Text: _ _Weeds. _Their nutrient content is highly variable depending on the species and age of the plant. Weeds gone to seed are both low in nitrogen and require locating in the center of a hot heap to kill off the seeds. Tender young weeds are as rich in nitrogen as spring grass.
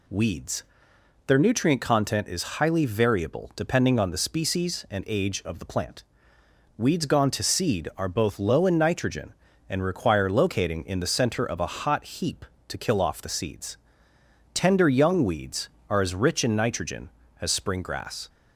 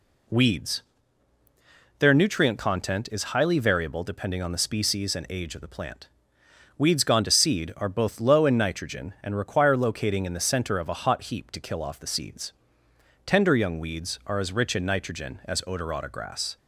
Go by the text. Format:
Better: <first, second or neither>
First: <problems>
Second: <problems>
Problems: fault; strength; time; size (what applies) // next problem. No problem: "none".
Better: first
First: none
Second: says "odorata" for "spring"; at 15.6 s